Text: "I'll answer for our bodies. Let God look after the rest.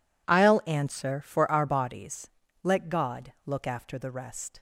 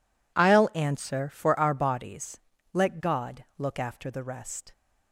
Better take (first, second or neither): neither